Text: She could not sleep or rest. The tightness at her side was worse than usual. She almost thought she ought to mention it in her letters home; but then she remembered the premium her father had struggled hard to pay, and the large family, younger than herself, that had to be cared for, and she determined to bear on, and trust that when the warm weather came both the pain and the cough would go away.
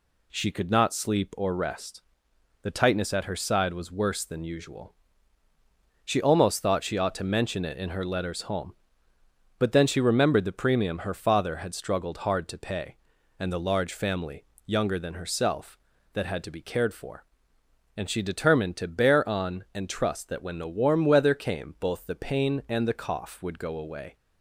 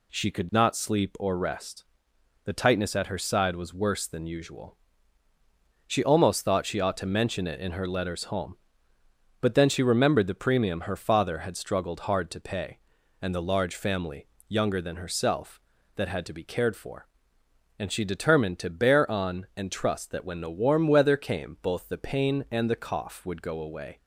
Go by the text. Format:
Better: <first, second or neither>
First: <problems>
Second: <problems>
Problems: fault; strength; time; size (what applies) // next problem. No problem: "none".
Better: neither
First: none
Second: none